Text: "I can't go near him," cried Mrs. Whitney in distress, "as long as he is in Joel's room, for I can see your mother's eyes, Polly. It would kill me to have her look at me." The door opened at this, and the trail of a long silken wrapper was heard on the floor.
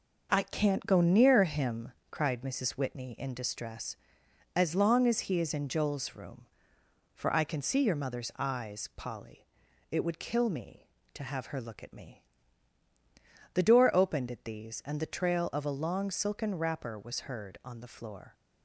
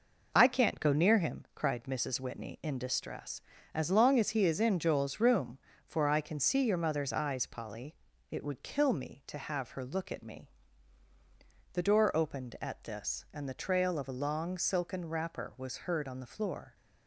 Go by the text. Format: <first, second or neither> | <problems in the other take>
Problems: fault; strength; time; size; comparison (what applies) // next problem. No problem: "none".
second | says "these" for "this"; at 14.4 s